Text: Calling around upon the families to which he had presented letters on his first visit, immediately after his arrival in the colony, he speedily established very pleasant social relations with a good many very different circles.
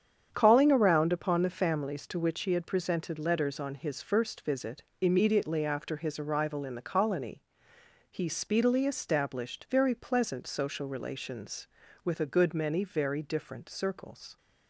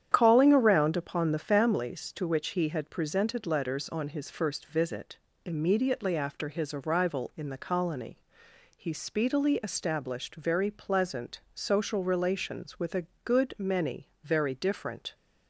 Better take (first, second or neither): first